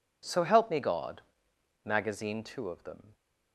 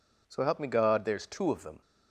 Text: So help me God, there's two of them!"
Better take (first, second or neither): second